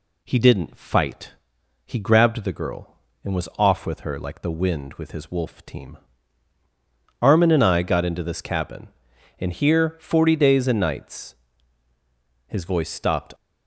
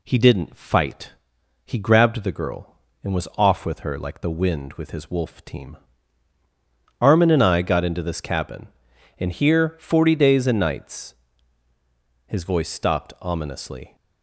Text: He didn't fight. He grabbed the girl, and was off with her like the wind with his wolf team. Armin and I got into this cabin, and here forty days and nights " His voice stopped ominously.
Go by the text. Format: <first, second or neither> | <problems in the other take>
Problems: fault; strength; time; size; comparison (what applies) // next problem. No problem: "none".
second | stops before "ominously"; at 13.3 s